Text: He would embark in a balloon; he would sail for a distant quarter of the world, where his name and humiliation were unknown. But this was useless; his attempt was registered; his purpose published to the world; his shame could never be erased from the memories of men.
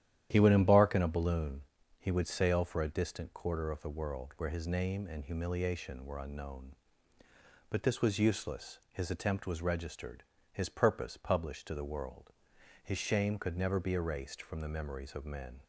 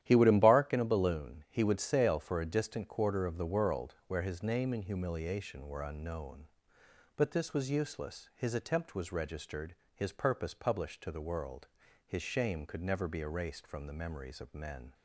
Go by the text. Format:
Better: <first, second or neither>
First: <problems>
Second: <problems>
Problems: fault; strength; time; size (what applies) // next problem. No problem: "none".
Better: neither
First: starts louder than the rest; strong; until 1.3 s; 11 dB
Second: starts louder than the rest; strong; until 1.0 s; 11.5 dB